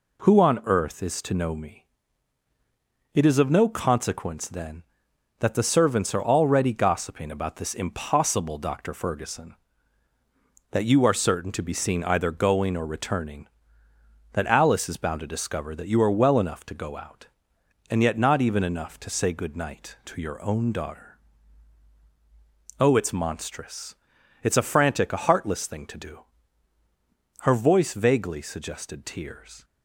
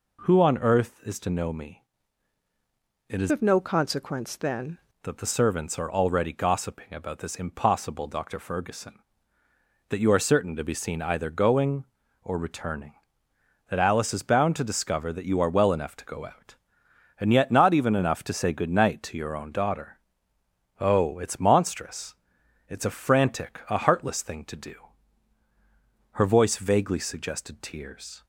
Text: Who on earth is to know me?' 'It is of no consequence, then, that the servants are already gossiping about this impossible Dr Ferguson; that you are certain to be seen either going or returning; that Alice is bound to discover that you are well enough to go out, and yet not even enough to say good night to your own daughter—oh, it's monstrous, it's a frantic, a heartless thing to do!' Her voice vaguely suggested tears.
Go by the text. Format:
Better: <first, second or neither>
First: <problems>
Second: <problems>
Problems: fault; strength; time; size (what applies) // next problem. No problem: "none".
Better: first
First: none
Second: changes voice from "of" to "then"; from 3.3 to 4.7 s; 1.4 s long